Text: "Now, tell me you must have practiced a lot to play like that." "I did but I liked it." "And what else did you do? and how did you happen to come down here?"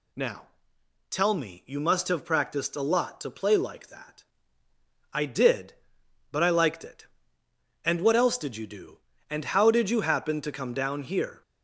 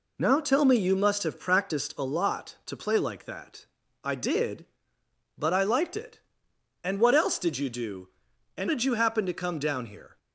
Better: first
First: none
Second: skips "how"; at 8.6 s

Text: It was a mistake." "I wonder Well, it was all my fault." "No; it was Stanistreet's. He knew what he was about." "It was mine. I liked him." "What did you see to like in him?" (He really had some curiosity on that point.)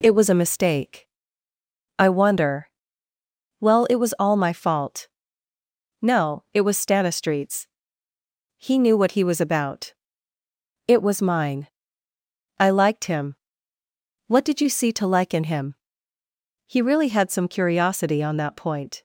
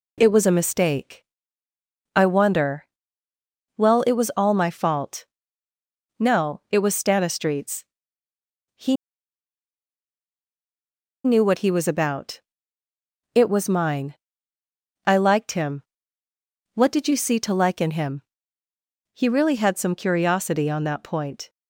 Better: first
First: pauses between "wonder" and "Well"; noticeable; at 2.6 s; 0.94 s long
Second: pauses between "wonder" and "Well"; noticeable; at 2.8 s; 0.94 s long // pauses between "He" and "knew"; strong; at 8.9 s; 2.2 s long

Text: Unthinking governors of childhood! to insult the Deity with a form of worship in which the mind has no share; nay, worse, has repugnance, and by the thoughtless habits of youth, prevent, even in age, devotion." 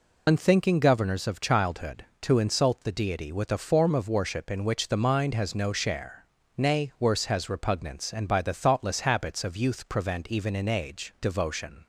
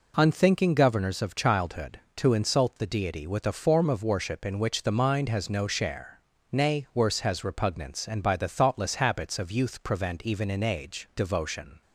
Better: second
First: loses the start of "Unthinking"; at 0.2 s; 80 ms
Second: none

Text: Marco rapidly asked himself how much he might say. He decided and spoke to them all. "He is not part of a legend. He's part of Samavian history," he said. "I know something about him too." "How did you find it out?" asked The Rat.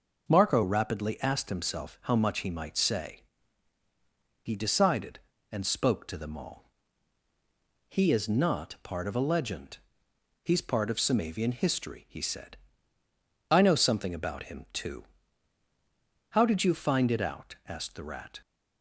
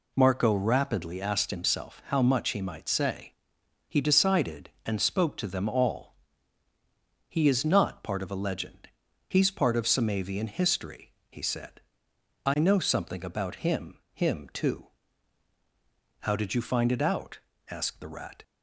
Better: first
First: none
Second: says "him" twice; at 14.1 s

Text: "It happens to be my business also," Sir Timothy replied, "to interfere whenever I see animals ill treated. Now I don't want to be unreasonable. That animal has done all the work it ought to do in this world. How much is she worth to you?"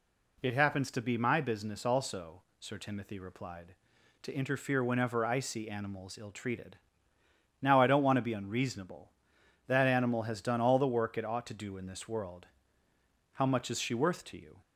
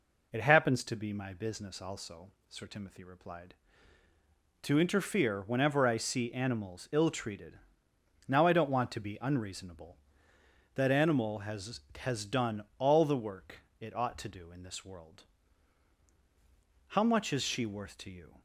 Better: first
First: none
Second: says "has" twice; at 12.0 s // pauses between "work" and "it"; slight; at 13.6 s; 0.18 s long

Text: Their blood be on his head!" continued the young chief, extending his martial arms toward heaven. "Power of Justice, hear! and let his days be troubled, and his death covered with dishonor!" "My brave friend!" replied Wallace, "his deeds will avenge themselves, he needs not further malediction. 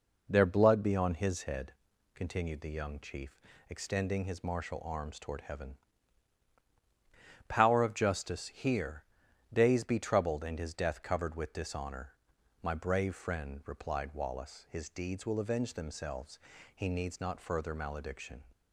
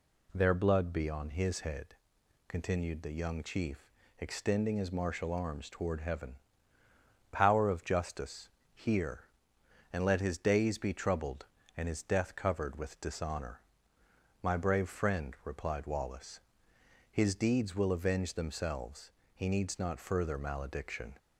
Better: second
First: skips "and let his"; at 9.2 s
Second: none

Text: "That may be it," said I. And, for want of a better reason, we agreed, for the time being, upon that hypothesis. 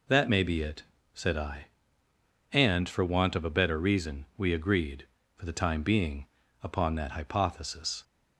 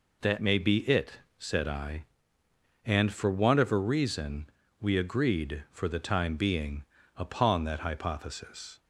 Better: first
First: none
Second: skips "better"; at 3.7 s

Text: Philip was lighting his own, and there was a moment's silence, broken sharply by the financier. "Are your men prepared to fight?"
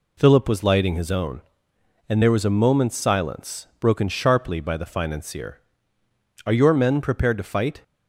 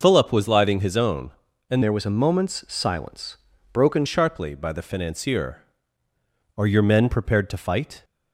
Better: first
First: none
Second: changes voice from "there" to "broken"; from 1.8 to 4.0 s; 2.2 s long

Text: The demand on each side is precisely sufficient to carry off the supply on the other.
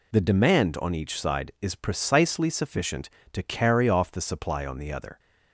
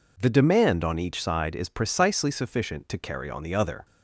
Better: first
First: none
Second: skips "off the supply"; at 3.2 s

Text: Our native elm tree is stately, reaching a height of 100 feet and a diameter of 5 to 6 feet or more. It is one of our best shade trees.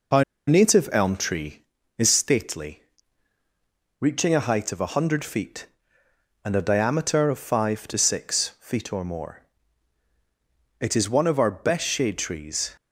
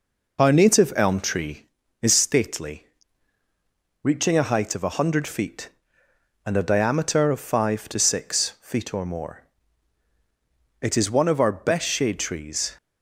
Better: second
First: pauses between "Our" and "native"; slight; at 0.2 s; 0.26 s long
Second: none

